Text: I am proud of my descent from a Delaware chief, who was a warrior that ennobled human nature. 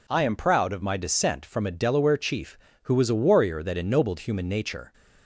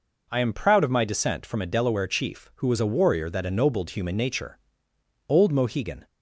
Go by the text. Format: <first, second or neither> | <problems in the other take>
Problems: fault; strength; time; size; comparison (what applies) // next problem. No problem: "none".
first | goes on to say "Old Mohegan"; noticeable; from 5.2 s on; 0.78 s long